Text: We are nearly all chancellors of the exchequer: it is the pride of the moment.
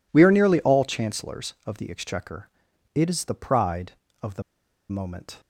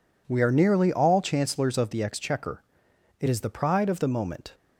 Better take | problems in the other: second | pauses between "the" and "moment"; noticeable; at 4.4 s; 0.47 s long

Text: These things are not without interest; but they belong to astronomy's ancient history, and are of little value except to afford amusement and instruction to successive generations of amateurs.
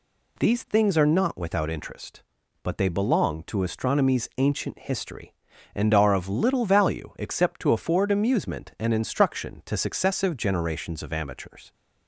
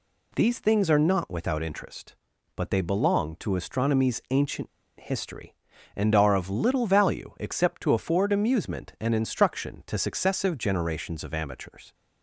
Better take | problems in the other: first | pauses between "ancient" and "history"; slight; at 4.6 s; 0.31 s long

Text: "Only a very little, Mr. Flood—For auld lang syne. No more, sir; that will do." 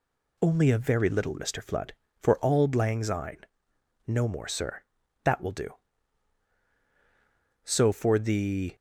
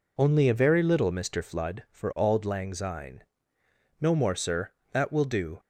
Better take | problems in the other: second | goes on to say "So for the"; noticeable; from 7.6 s on; 1.1 s long

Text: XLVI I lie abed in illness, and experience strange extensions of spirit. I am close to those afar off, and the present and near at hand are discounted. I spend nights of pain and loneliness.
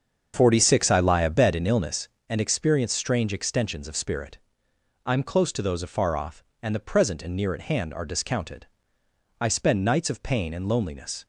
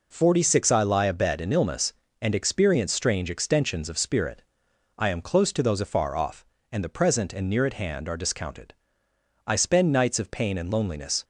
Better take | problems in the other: second | starts louder than the rest; until 2.0 s; 7 dB

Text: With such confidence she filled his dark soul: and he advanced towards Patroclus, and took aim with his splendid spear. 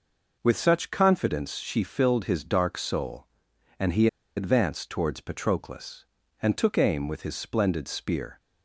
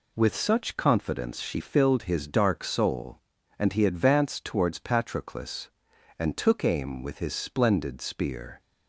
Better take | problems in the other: second | pauses between "he" and "advanced"; slight; at 4.0 s; 0.30 s long

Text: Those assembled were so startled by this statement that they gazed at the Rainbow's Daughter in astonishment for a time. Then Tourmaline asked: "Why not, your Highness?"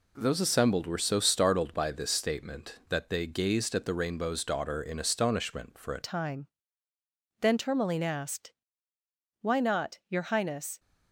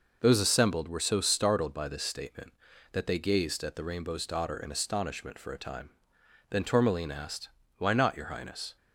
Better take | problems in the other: second | changes voice at "time"; from 6.0 s on; 4.7 s long

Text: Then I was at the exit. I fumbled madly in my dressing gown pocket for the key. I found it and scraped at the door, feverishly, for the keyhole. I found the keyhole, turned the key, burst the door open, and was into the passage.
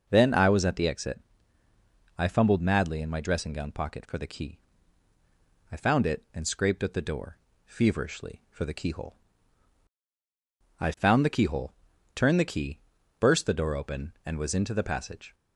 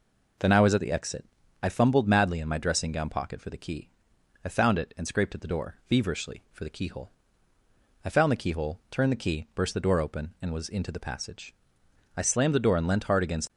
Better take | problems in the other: first | goes on to say "I slammed the door and leant hard against"; from 12.1 s on; 1.3 s long

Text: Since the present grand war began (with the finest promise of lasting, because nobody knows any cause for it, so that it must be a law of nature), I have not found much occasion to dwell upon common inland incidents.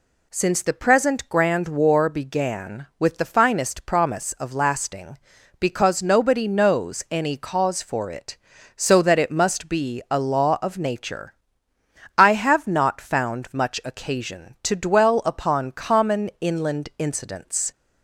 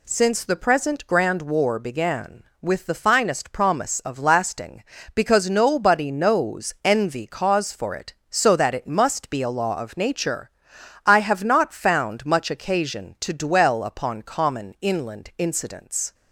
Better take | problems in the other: first | says "envy" for "any"; at 6.8 s

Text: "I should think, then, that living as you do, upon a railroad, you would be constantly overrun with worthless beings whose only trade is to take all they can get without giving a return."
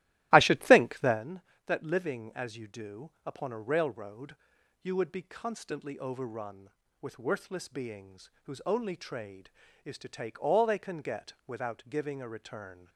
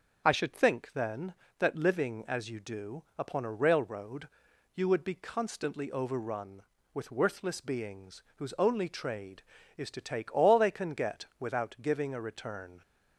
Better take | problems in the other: second | starts louder than the rest; strong; until 1.2 s; 15.5 dB // pauses between "get" and "without"; slight; at 11.3 s; 0.16 s long; slight in the second

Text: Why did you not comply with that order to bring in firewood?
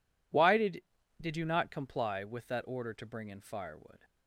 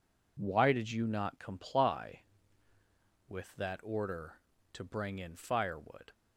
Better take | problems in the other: second | says "did" twice; at 1.2 s

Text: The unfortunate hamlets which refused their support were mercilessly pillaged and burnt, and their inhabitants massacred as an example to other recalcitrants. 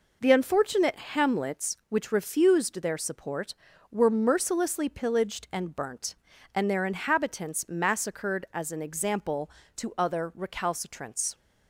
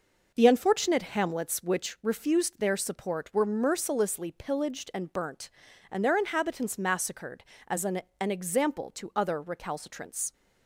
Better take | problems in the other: first | says "an" twice; at 8.1 s

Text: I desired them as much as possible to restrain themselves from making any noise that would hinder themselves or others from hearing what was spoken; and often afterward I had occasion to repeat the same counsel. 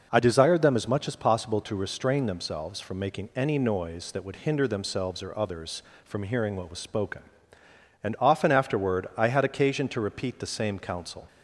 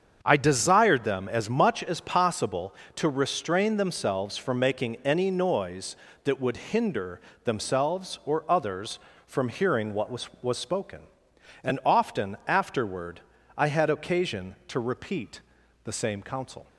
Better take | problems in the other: first | starts louder than the rest; strong; until 1.2 s; 7 dB // pauses between "hinder" and "themselves"; slight; at 7.1 s; 0.24 s long // says "was" twice; at 10.4 s // pauses between "afterward" and "I"; slight; at 13.2 s; 0.36 s long // pauses between "repeat" and "the"; noticeable; at 15.3 s; 0.46 s long

